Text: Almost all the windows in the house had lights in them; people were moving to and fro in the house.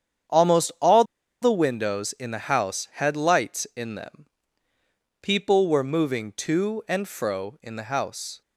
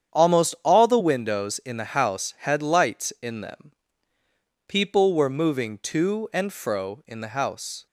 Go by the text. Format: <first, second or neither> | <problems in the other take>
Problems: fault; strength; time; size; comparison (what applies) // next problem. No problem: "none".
second | starts louder than the rest; strong; until 1.7 s; 8.5 dB; strong in the second // pauses between "all" and "the"; at 1.0 s; 0.38 s long